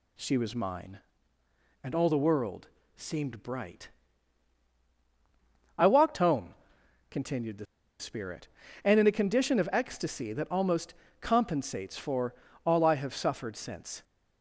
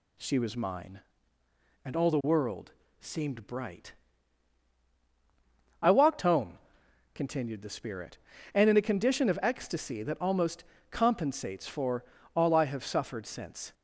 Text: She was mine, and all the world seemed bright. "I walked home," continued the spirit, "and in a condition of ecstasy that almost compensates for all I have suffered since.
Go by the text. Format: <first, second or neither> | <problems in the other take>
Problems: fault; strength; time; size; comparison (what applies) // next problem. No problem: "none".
second | pauses between "world" and "seemed"; slight; at 2.6 s; 0.28 s long; slight in the second // pauses between "the" and "spirit"; slight; at 7.6 s; 0.34 s long // pauses between "almost" and "compensates"; slight; at 10.9 s; 0.28 s long; slight in the second // pauses between "for" and "all"; slight; at 12.3 s; 0.30 s long; slight in the second